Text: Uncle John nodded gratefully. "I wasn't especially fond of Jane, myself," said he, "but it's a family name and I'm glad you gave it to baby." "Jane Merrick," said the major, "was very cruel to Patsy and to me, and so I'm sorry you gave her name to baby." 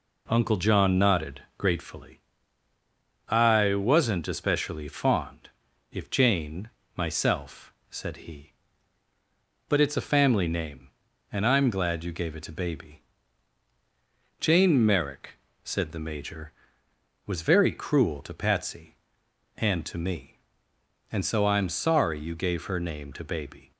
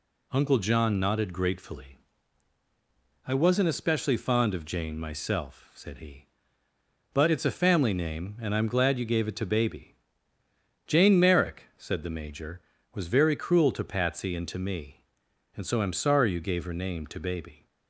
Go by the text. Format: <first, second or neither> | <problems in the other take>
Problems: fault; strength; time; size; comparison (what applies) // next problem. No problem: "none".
second | says "if" for "of"; at 5.9 s